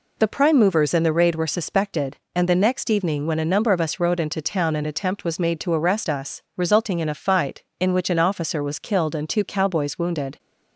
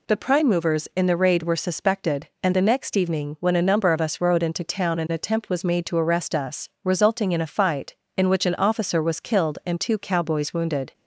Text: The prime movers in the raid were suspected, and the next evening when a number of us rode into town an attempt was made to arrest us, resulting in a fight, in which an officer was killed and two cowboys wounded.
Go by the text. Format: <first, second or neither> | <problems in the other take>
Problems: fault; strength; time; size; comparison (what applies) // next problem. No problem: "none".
neither | none